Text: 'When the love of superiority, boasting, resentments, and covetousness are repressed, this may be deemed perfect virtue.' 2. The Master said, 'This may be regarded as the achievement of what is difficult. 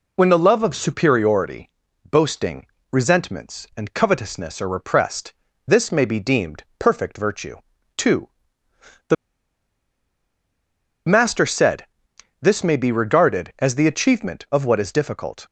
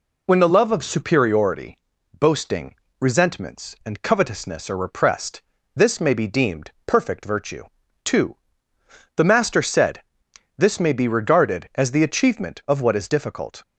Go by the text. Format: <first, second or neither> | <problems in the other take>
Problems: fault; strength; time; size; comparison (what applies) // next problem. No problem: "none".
second | pauses between "deemed" and "perfect"; slight; at 6.6 s; 0.16 s long; slight in the second // pauses between "The" and "Master"; strong; at 9.1 s; 1.9 s long